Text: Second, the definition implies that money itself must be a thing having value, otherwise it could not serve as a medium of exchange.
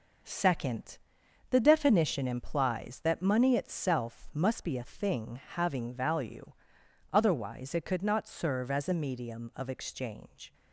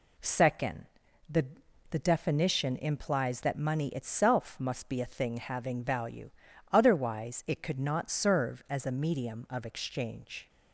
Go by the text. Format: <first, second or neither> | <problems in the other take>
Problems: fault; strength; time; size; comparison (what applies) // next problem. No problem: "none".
first | says "the" twice; at 1.9 s